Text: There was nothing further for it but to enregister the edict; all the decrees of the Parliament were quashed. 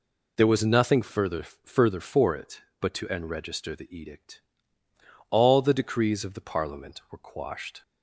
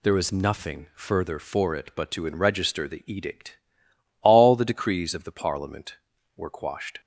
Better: second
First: says "further" twice; at 1.4 s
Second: none

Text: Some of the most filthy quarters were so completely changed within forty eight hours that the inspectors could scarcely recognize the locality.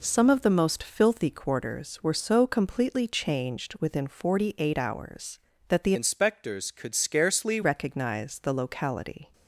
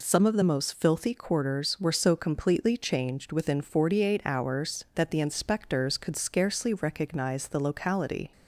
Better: second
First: changes voice from "inspectors" to "scarcely"; from 5.9 to 7.6 s; 1.7 s long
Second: none

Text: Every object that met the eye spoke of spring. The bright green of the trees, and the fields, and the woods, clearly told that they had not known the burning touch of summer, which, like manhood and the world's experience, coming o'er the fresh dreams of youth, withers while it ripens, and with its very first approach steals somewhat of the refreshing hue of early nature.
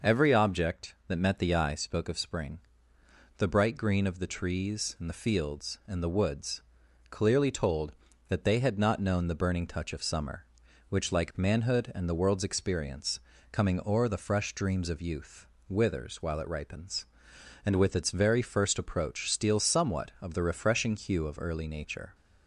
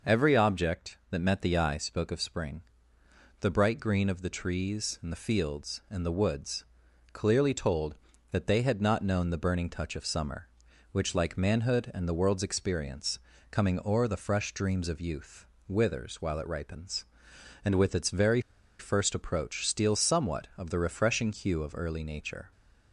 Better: first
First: none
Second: pauses between "very" and "first"; at 18.3 s; 0.39 s long

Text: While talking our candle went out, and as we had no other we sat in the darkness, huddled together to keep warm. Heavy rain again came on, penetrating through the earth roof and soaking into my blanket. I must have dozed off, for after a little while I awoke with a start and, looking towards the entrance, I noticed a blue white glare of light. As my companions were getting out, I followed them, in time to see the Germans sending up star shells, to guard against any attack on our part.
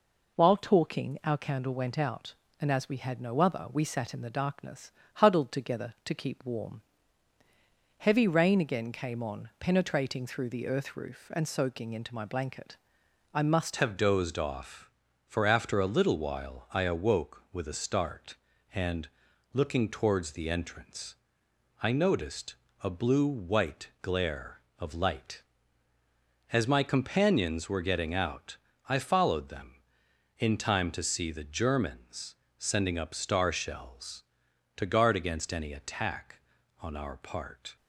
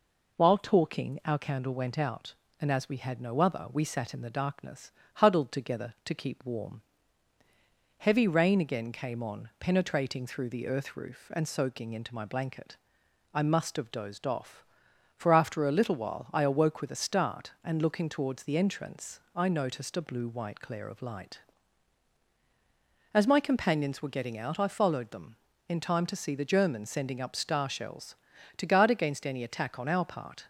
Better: second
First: changes voice at "have"; from 13.7 s on; 24.0 s long // pauses between "noticed" and "a"; slight; at 22.5 s; 0.30 s long // pauses between "Germans" and "sending"; slight; at 32.3 s; 0.22 s long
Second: none

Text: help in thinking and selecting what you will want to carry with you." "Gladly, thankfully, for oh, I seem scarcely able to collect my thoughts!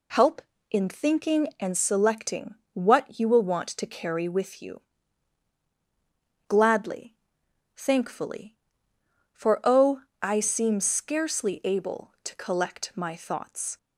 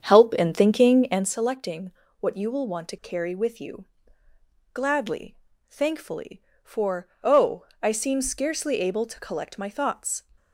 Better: first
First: pauses between "selecting" and "what"; slight; at 2.5 s; 0.20 s long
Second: starts louder than the rest; strong; until 1.3 s; 8 dB // pauses between "selecting" and "what"; slight; at 1.9 s; 0.28 s long // pauses between "for" and "oh"; slight; at 7.0 s; 0.16 s long

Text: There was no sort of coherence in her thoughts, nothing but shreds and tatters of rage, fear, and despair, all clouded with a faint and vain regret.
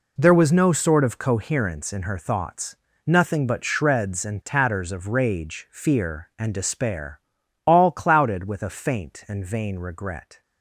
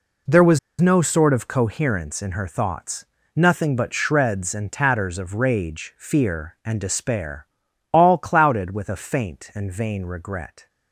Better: first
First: none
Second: pauses between "was" and "no"; slight; at 0.5 s; 0.21 s long

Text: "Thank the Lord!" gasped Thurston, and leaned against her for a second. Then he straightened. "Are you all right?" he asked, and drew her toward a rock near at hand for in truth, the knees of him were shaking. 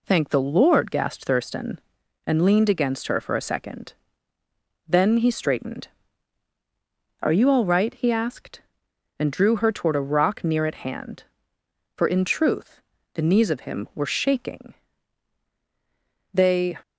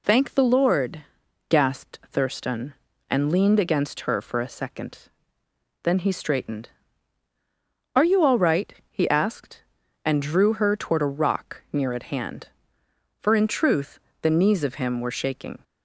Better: second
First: goes on to say "They"; slight; from 16.3 s on; 0.42 s long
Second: none

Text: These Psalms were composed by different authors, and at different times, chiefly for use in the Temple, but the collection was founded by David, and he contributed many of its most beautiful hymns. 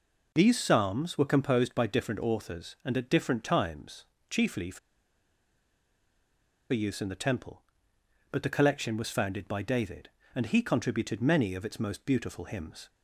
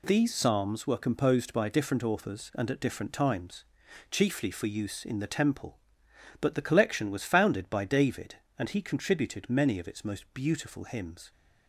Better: second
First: pauses between "for" and "use"; strong; at 4.7 s; 1.9 s long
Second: none

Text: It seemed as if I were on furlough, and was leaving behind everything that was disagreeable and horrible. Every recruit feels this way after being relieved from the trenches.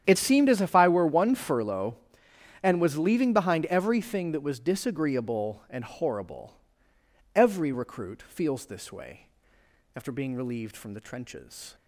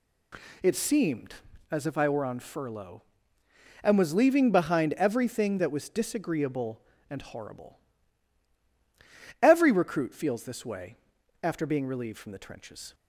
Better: second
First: starts louder than the rest; strong; until 1.0 s; 9 dB // says "one" for "on"; at 1.0 s // pauses between "way" and "after"; noticeable; at 9.2 s; 0.70 s long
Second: pauses between "way" and "after"; noticeable; at 10.9 s; 0.46 s long

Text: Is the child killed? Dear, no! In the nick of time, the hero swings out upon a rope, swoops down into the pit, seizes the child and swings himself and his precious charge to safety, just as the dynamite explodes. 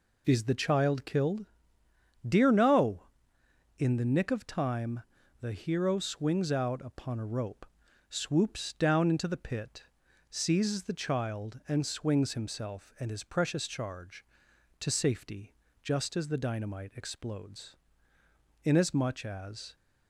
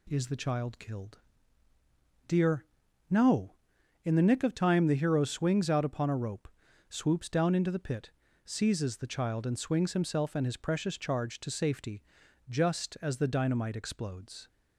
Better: second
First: goes on to say "Inasmuch as"; noticeable; from 18.6 s on; 1.1 s long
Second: none

